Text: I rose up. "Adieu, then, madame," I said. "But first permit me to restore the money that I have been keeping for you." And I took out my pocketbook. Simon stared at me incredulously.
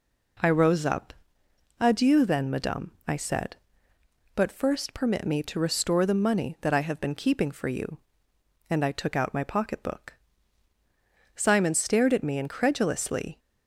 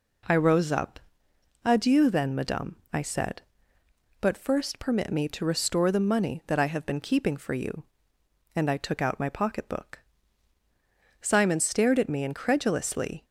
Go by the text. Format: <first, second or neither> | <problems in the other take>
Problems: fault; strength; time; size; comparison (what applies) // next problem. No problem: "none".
neither | none